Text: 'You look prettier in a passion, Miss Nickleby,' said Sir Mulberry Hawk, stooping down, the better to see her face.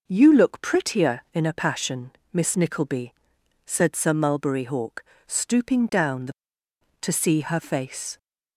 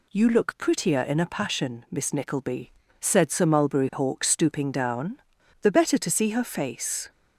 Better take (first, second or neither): second